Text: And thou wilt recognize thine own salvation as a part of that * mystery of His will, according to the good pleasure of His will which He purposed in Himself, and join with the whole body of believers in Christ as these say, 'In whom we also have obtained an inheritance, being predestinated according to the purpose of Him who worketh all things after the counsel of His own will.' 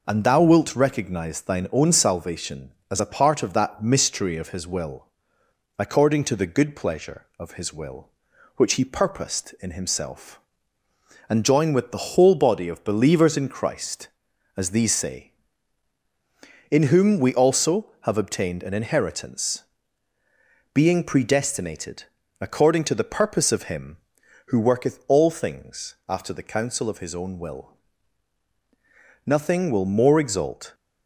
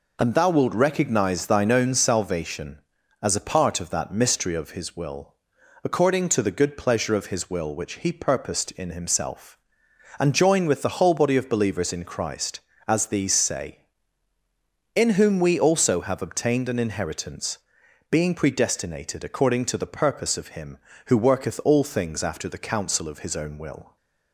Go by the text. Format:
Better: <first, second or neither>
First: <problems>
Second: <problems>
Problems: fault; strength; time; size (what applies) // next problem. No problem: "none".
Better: second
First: pauses between "predestinated" and "according"; slight; at 22.0 s; 0.36 s long // goes on to say "Nothing will more exalt"; from 29.2 s on; 1.4 s long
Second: none